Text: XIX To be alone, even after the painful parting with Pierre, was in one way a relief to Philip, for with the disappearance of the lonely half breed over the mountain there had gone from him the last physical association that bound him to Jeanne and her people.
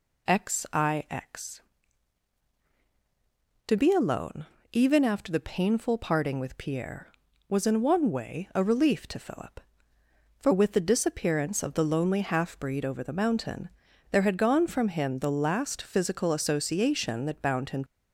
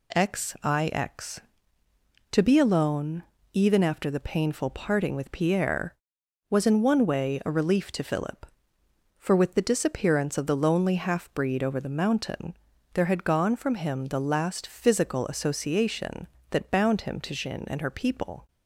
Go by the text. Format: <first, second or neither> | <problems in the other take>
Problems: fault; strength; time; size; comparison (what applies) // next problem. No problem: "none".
second | pauses between "mountain" and "there"; at 13.6 s; 0.42 s long; also in the second // stops before "to Jeanne and her people"; at 17.8 s